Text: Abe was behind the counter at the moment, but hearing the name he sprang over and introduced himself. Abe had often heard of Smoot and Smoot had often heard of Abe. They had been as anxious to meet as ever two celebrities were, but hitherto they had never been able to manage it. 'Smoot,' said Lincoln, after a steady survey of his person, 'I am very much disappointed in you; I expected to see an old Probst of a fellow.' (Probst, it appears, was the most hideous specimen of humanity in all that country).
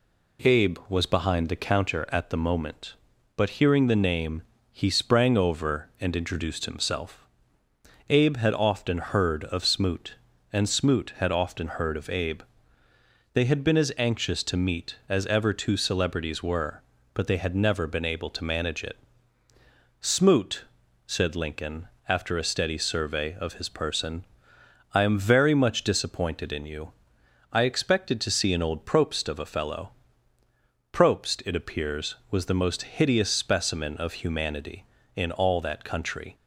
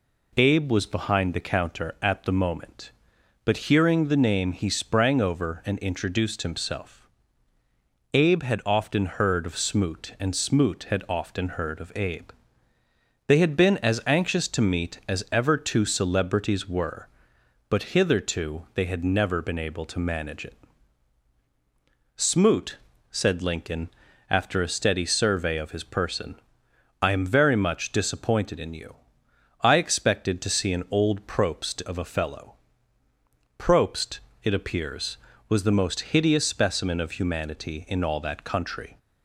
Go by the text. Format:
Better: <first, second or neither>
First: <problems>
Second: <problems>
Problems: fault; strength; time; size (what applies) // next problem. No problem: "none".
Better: second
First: pauses between "name" and "he"; slight; at 4.4 s; 0.32 s long // skips "hitherto"; at 17.2 s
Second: none